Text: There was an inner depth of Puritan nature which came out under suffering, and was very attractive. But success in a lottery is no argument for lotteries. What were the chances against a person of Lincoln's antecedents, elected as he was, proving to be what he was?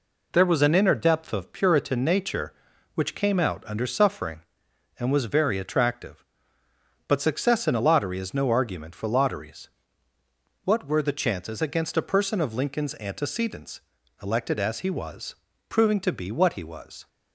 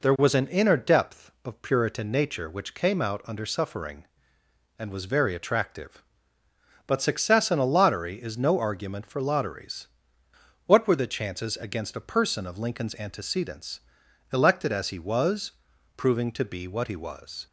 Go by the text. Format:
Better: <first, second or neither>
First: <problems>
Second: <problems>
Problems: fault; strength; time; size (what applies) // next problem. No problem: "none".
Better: neither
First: none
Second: none